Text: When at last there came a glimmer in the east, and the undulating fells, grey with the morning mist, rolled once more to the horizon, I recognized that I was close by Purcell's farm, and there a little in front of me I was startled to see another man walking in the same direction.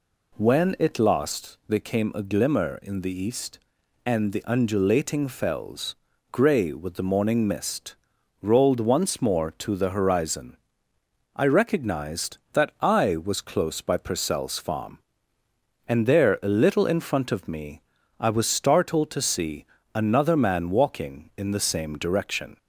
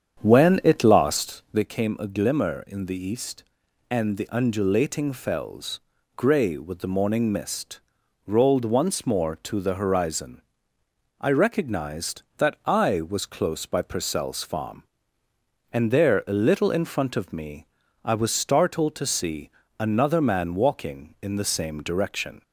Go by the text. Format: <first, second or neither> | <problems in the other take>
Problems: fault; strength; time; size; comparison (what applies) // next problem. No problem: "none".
first | starts louder than the rest; strong; until 1.6 s; 8 dB // pauses between "me" and "I"; at 17.6 s; 0.38 s long; also in the first // pauses between "see" and "another"; slight; at 19.5 s; 0.28 s long; slight in the first